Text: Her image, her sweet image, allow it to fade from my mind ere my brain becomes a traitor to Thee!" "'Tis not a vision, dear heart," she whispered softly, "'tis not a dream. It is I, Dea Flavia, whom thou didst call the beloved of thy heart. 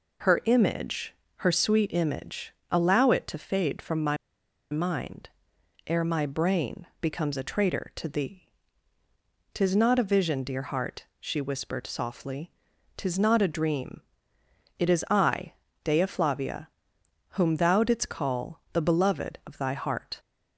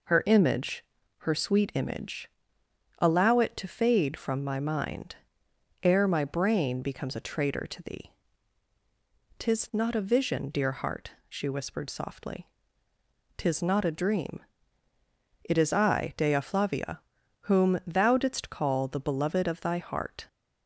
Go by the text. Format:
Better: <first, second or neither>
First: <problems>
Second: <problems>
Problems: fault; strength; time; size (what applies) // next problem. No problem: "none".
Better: second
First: pauses between "my" and "mind"; noticeable; at 4.1 s; 0.55 s long // pauses between "mind" and "ere"; noticeable; at 5.2 s; 0.58 s long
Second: pauses between "mind" and "ere"; noticeable; at 5.1 s; 0.66 s long